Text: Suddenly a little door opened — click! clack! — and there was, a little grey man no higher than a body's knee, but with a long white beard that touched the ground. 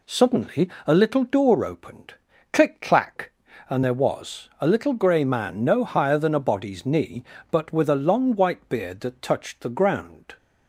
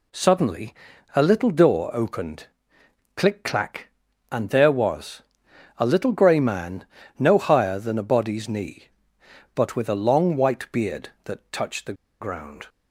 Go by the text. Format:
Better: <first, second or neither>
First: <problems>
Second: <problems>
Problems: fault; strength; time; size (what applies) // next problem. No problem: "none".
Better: first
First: pauses between "Suddenly" and "a"; slight; at 0.6 s; 0.16 s long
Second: pauses between "Suddenly" and "a"; at 0.7 s; 0.40 s long // pauses between "man" and "no"; slight; at 6.8 s; 0.32 s long // pauses between "the" and "ground"; slight; at 11.9 s; 0.27 s long